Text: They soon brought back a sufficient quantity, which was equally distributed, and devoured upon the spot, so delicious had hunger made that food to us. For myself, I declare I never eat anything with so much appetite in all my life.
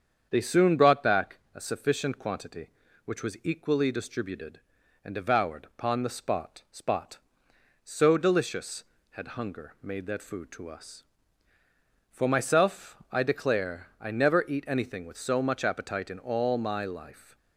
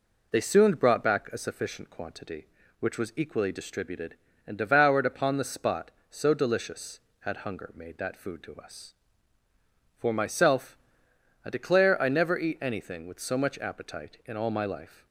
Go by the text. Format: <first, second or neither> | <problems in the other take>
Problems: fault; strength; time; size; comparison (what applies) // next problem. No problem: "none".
second | starts louder than the rest; strong; until 1.3 s; 7.5 dB // pauses between "back" and "a"; slight; at 1.3 s; 0.16 s long // says "spot" twice; at 6.7 s